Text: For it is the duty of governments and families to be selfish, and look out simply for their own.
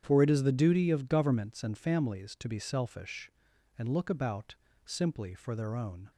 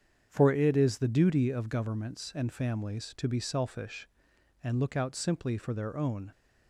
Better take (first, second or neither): second